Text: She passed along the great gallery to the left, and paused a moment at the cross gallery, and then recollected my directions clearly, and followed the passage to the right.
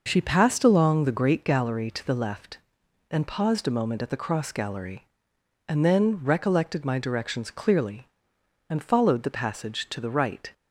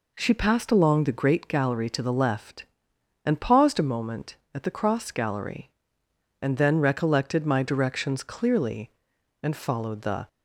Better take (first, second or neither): first